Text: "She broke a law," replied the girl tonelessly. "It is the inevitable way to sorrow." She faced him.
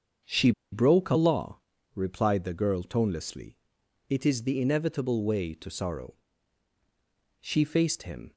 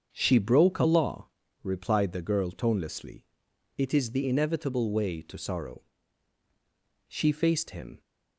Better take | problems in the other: second | starts louder than the rest; until 1.4 s; 7 dB; also in the second // pauses between "She" and "broke"; slight; at 0.5 s; 0.21 s long

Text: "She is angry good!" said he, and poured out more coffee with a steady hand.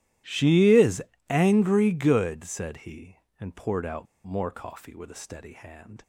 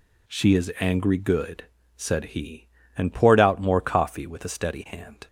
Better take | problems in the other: second | starts louder than the rest; strong; until 1.5 s; 14.5 dB // pauses between "is" and "angry"; slight; at 1.0 s; 0.24 s long // pauses between "out" and "more"; slight; at 4.0 s; 0.20 s long

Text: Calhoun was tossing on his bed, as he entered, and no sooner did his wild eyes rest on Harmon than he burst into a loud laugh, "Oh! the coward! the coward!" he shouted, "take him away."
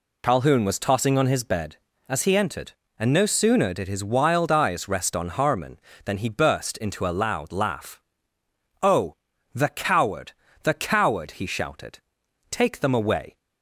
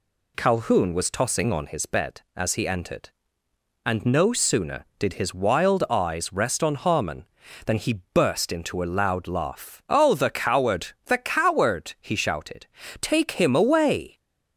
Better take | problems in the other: second | says "them" for "him"; at 12.8 s

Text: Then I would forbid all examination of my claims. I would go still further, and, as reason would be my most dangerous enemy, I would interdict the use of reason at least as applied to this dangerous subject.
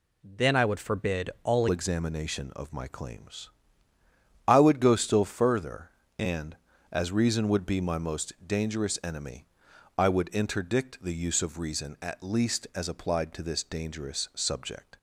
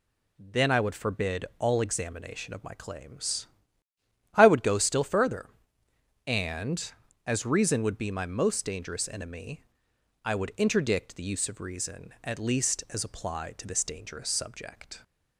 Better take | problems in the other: second | changes voice at "examination"; from 1.6 s on; 13.3 s long

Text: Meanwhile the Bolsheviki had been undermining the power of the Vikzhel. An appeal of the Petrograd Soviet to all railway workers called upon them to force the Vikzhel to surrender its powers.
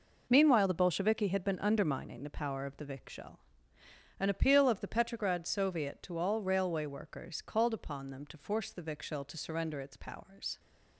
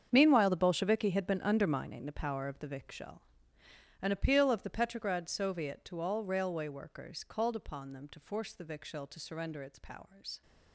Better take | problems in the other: first | gets quieter; strong; throughout; 15 dB

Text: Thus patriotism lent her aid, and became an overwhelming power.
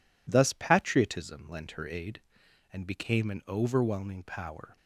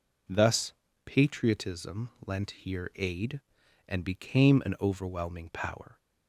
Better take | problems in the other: first | pauses between "Thus" and "patriotism"; slight; at 0.7 s; 0.32 s long // pauses between "patriotism" and "lent"; slight; at 2.0 s; 0.16 s long // says "here" for "her"; at 2.5 s

